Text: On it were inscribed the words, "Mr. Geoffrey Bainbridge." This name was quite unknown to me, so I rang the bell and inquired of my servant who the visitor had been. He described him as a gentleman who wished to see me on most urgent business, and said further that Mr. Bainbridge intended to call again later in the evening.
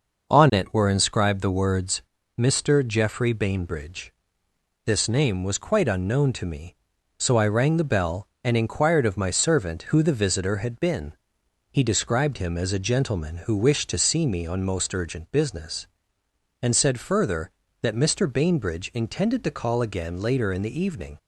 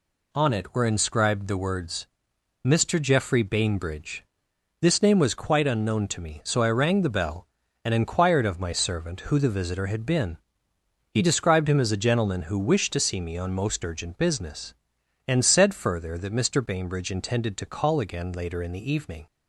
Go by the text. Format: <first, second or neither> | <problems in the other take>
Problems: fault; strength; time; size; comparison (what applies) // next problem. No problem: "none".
neither | none